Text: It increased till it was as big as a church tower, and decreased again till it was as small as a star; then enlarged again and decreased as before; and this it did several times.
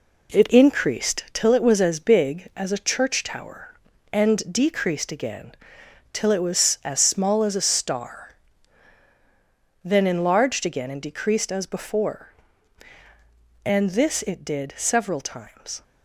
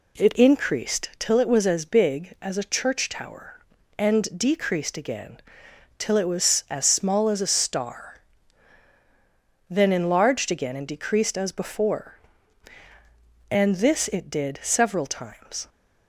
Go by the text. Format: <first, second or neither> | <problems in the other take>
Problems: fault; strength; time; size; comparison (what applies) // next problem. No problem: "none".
second | gets quieter; throughout; 6.5 dB // pauses between "again" and "till"; noticeable; at 5.5 s; 0.60 s long; noticeable in the second